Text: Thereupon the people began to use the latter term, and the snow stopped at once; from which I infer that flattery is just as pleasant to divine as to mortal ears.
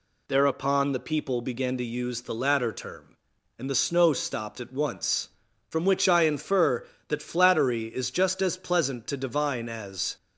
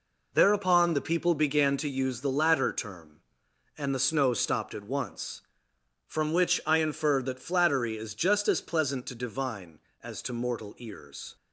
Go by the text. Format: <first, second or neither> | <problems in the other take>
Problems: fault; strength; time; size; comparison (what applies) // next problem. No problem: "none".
second | stops before "to mortal ears"; at 10.1 s